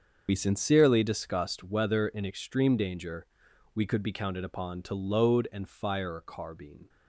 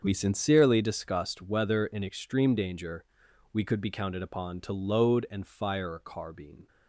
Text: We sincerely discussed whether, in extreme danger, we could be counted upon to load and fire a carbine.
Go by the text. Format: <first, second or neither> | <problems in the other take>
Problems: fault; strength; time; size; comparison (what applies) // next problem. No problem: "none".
second | loses the start of "We"; at 0.2 s; 50 ms // starts louder than the rest; until 1.2 s; 6.5 dB; also in the second